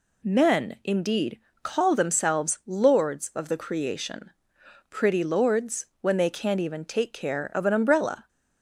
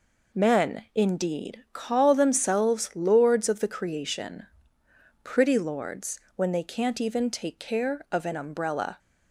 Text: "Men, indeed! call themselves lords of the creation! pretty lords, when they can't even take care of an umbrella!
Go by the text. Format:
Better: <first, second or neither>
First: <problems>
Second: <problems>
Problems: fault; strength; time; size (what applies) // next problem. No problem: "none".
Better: neither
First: none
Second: none